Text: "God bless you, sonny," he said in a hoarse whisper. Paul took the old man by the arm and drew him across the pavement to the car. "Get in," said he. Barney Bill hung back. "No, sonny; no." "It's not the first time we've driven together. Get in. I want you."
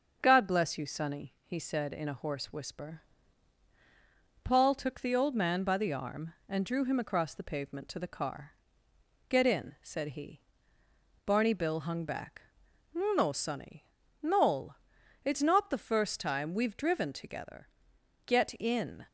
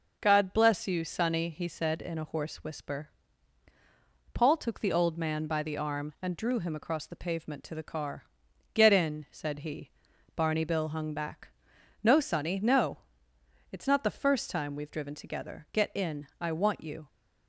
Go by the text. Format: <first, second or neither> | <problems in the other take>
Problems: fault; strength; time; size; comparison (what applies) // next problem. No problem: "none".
second | starts louder than the rest; until 1.2 s; 6.5 dB // stops before "I want you"; at 19.0 s